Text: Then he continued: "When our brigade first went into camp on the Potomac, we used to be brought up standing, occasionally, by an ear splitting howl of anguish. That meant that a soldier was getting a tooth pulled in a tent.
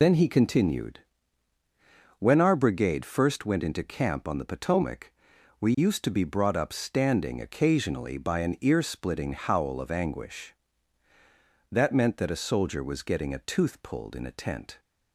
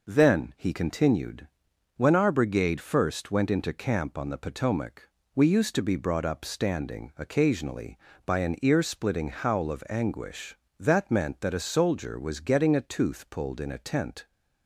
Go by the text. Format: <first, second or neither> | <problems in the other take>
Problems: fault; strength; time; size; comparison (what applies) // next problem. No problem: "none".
second | loses the start of "Then"; at 0.0 s; 65 ms